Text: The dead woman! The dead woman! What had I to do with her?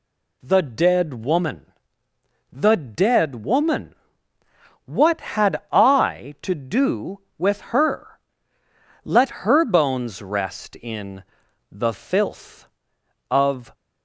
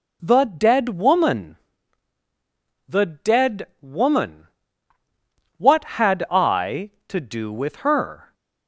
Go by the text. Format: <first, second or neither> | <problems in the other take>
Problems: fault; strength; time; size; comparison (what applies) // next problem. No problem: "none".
second | goes on to say "Let her bones rest in the filth of"; strong; from 9.0 s on; 4.7 s long